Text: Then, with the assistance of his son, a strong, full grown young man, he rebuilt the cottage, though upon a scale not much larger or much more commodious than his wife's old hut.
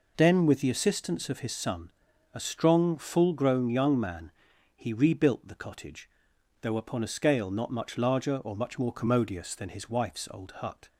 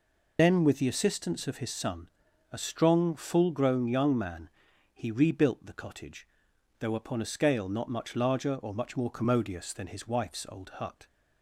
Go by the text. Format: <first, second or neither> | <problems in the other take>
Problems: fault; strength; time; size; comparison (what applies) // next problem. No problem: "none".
first | loses the start of "Then"; at 0.3 s; 45 ms